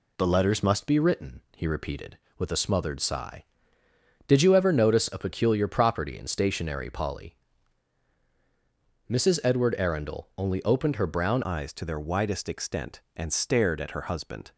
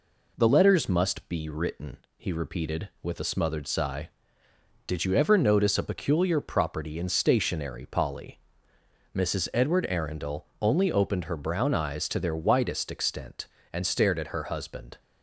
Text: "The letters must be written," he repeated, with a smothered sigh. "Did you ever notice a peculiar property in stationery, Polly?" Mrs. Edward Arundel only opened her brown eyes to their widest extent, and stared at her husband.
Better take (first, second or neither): second